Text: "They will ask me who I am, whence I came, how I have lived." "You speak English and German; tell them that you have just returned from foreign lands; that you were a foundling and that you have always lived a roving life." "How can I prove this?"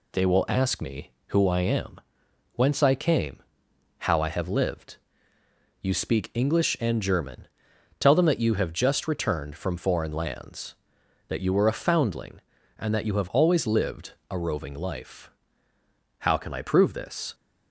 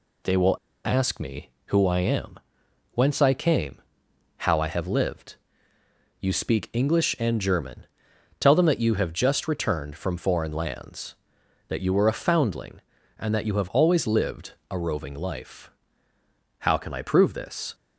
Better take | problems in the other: first | pauses between "will" and "ask"; slight; at 0.5 s; 0.27 s long // pauses between "lived" and "a"; slight; at 14.5 s; 0.16 s long; slight in the first

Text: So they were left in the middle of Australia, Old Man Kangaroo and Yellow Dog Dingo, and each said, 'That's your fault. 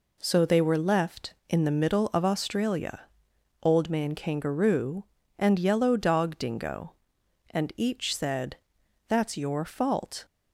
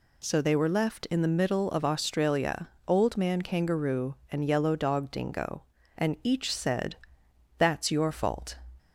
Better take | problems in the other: neither | none

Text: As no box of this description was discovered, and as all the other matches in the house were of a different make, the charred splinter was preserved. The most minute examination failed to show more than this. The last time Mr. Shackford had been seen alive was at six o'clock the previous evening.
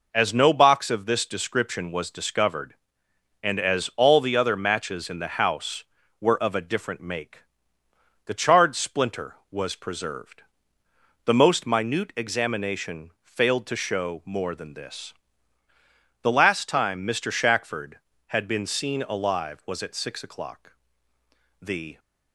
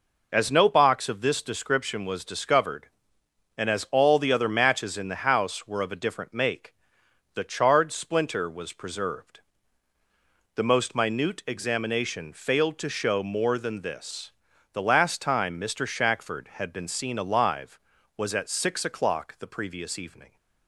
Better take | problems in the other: second | pauses between "o'clock" and "the"; noticeable; at 20.7 s; 0.88 s long // stops before "previous evening"; at 21.9 s

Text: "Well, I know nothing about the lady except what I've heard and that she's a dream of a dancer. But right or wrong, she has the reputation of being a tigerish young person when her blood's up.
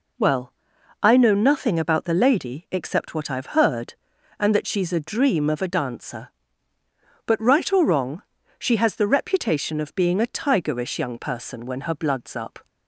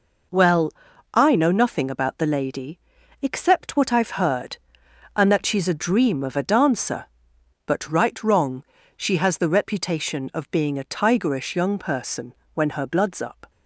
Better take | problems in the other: first | pauses between "lady" and "except"; at 2.7 s; 0.44 s long // skips "or"; at 8.2 s // pauses between "person" and "when"; slight; at 12.3 s; 0.20 s long

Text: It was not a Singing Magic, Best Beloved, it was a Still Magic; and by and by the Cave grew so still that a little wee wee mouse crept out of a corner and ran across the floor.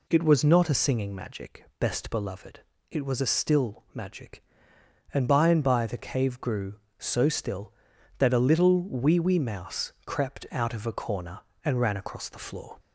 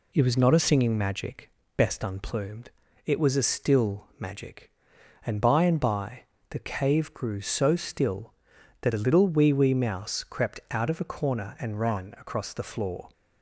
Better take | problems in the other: first | says "Unplumed" for "Beloved"; at 2.0 s // pauses between "by" and "the"; slight; at 6.2 s; 0.26 s long

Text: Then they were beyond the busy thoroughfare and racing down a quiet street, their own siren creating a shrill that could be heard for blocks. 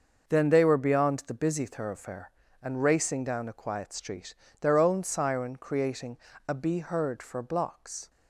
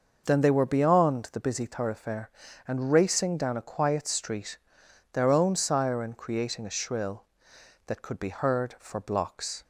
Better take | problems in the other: second | starts louder than the rest; noticeable; until 1.2 s; 6 dB // pauses between "creating" and "a"; slight; at 6.1 s; 0.30 s long // skips "shrill that could"; at 6.5 s

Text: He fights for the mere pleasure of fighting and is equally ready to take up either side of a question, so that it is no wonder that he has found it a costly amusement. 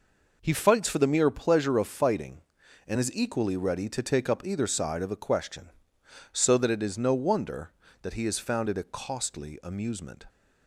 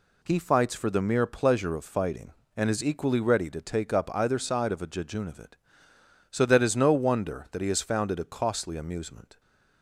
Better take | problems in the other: first | says "jejunavit" for "question"; at 4.8 s

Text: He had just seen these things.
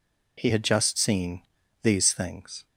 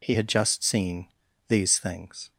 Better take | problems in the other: neither | pauses between "seen" and "these"; the same in both

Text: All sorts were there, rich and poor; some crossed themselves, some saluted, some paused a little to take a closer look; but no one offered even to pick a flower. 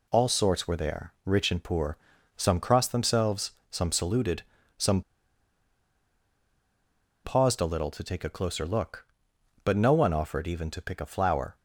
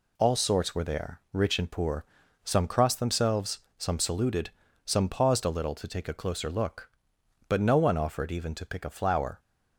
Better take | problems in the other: second | pauses between "some" and "paused"; strong; at 5.0 s; 2.2 s long

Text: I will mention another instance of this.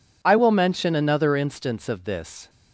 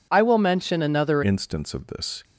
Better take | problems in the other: first | changes voice at "instance"; from 1.2 s on; 1.0 s long

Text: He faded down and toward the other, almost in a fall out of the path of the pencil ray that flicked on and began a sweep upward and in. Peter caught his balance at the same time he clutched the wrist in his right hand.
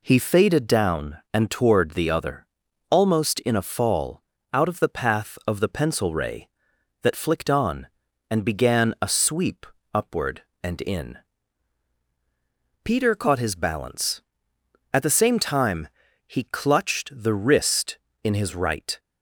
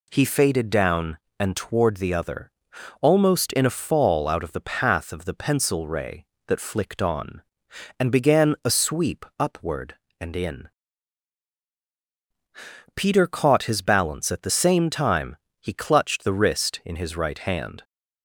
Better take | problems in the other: second | pauses between "fall" and "out"; slight; at 4.2 s; 0.30 s long // pauses between "sweep" and "upward"; slight; at 9.6 s; 0.28 s long // pauses between "time" and "he"; at 15.8 s; 0.40 s long; slight in the second // stops before "hand"; at 18.9 s

